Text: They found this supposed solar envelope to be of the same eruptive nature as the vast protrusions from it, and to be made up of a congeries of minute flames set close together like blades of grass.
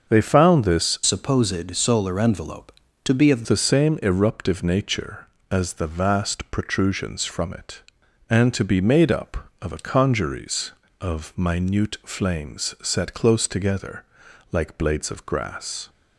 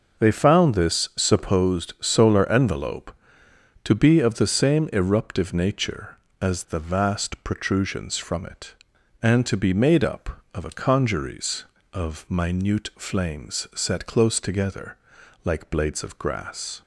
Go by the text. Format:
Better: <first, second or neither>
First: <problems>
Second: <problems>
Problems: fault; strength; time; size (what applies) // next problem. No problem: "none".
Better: second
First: starts louder than the rest; until 1.1 s; 6.5 dB // changes voice from "supposed" to "of"; from 1.0 to 3.4 s; 2.4 s long // pauses between "together" and "like"; noticeable; at 14.0 s; 0.48 s long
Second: starts louder than the rest; noticeable; until 1.2 s; 6 dB // pauses between "together" and "like"; noticeable; at 14.9 s; 0.48 s long